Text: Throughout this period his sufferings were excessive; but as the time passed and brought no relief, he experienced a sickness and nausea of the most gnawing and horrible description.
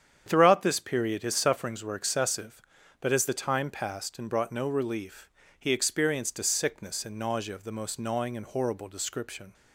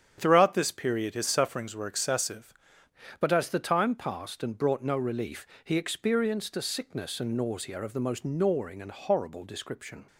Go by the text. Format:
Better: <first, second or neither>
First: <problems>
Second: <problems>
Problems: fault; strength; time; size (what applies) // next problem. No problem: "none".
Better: first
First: starts louder than the rest; strong; until 1.2 s; 8.5 dB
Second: starts louder than the rest; strong; until 1.1 s; 9 dB // changes voice at "but"; from 3.2 s on; 6.8 s long